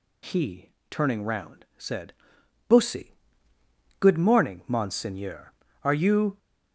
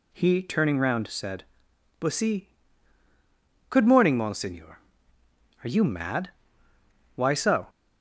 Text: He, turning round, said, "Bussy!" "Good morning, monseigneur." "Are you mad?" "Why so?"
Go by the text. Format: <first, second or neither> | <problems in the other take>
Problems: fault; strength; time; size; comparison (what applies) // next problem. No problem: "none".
second | stops before "mad Why so"; at 6.3 s